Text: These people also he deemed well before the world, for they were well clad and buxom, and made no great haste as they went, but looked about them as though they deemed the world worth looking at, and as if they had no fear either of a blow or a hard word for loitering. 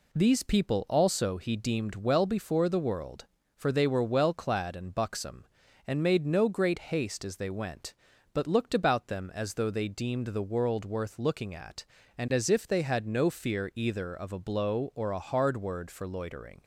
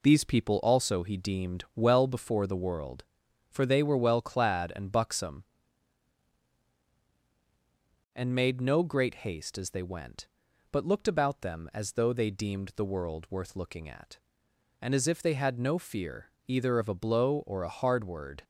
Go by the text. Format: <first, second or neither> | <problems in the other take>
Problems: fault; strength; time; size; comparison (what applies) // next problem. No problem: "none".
first | pauses between "fear" and "either"; slight; at 16.2 s; 0.18 s long // stops before "for loitering"; at 18.4 s